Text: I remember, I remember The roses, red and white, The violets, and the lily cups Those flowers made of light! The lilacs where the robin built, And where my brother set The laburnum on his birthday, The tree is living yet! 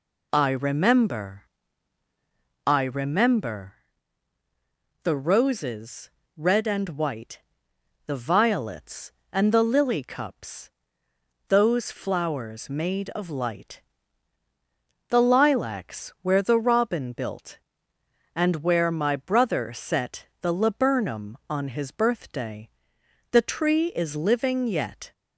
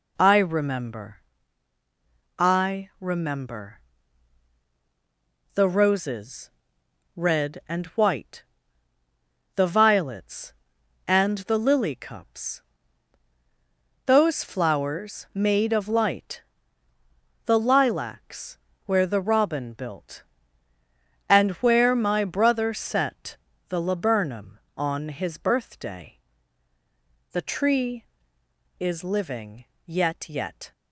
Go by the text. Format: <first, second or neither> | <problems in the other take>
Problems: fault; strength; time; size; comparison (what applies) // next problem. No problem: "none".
first | pauses between "remember" and "The"; strong; at 3.7 s; 1.7 s long; strong in the first // pauses between "cups" and "Those"; strong; at 12.6 s; 1.4 s long; noticeable in the first // pauses between "lilacs" and "where"; slight; at 18.5 s; 0.28 s long // pauses between "set" and "The"; slight; at 23.3 s; 0.32 s long; slight in the first // pauses between "living" and "yet"; slight; at 29.6 s; 0.22 s long // says "yet" twice; at 30.2 s